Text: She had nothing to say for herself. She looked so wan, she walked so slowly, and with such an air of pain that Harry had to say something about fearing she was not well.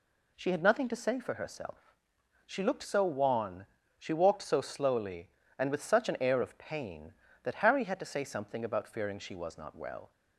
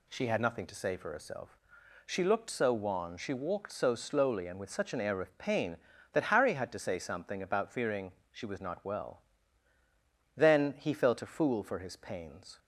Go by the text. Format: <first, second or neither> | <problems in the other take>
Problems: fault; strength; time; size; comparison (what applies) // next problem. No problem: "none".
first | pauses between "fearing" and "she"; slight; at 8.1 s; 0.20 s long // goes on to say "Then he felt a fool for his pains"; strong; from 10.3 s on; 2.2 s long